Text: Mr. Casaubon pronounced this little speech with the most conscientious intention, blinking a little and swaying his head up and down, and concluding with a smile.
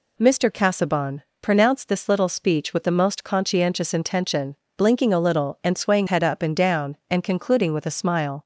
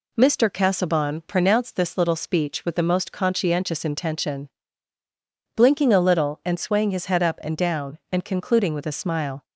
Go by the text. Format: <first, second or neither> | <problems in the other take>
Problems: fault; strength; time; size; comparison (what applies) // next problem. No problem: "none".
second | pauses between "Casaubon" and "pronounced"; slight; at 1.2 s; 0.22 s long // skips "his"; at 6.0 s